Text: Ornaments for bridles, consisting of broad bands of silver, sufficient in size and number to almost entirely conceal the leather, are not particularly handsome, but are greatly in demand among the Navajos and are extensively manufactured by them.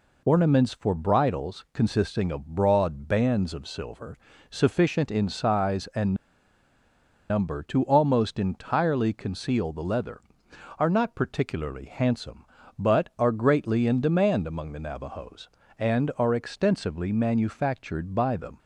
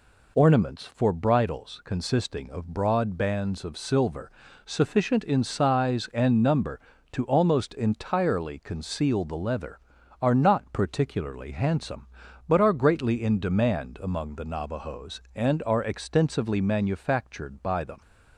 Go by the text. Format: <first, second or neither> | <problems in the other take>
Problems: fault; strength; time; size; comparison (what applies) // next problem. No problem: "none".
second | pauses between "and" and "number"; at 6.1 s; 1.1 s long